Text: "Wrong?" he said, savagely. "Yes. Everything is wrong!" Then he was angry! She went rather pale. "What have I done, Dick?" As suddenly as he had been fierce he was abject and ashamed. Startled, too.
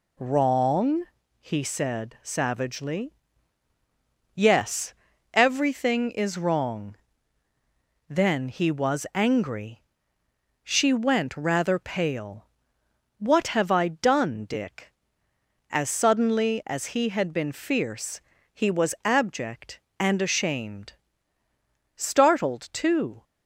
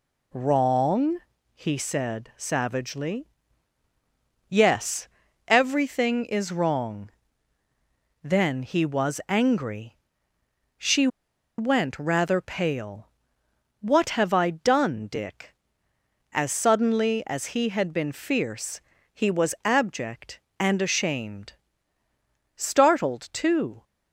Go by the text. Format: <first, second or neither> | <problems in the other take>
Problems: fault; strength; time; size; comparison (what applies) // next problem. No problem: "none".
first | pauses between "She" and "went"; noticeable; at 11.0 s; 0.50 s long // pauses between "fierce" and "he"; slight; at 18.7 s; 0.34 s long; slight in the first